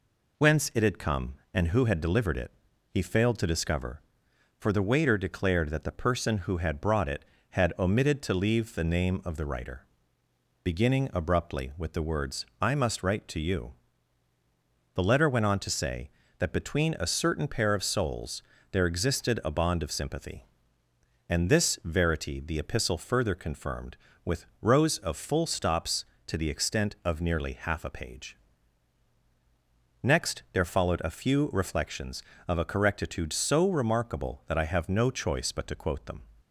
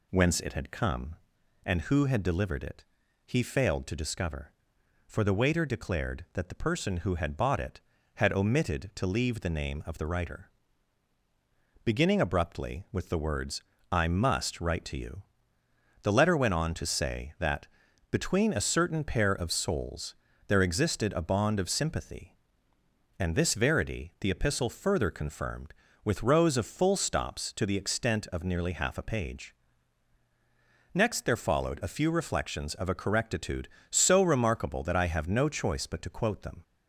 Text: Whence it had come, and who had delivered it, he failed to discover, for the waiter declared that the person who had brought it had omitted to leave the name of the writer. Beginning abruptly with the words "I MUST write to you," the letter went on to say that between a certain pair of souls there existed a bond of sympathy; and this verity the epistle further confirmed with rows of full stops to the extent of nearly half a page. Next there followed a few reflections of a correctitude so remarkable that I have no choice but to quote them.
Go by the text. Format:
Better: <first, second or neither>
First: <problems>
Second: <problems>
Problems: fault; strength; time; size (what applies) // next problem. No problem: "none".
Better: first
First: pauses between "words" and "I"; slight; at 12.4 s; 0.16 s long // pauses between "souls" and "there"; slight; at 18.4 s; 0.30 s long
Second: says "bought" for "brought"; at 7.3 s // pauses between "words" and "I"; slight; at 13.6 s; 0.28 s long // pauses between "that" and "between"; noticeable; at 17.6 s; 0.46 s long // pauses between "souls" and "there"; slight; at 20.1 s; 0.32 s long